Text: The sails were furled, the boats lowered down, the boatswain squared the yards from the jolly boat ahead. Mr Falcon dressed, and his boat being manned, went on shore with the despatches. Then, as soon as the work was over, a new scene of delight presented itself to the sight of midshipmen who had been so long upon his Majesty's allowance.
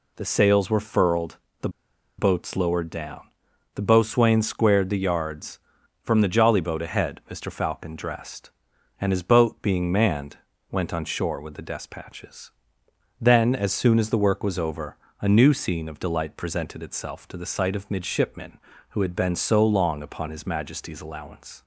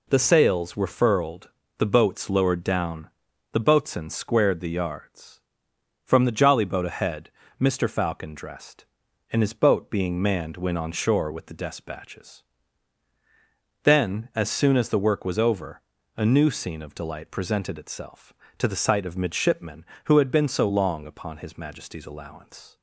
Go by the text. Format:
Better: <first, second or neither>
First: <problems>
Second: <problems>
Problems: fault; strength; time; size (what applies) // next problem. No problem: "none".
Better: second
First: pauses between "the" and "boats"; noticeable; at 1.6 s; 0.48 s long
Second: none